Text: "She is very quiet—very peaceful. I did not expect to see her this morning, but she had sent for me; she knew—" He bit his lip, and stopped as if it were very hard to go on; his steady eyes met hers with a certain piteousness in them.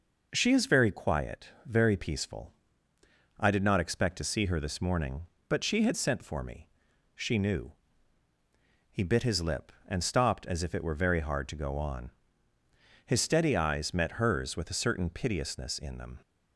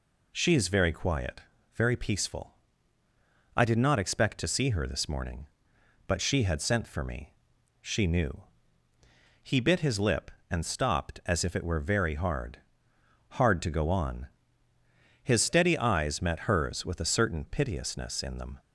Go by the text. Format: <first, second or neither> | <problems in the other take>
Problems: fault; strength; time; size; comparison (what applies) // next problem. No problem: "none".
first | says "hard" twice; at 13.3 s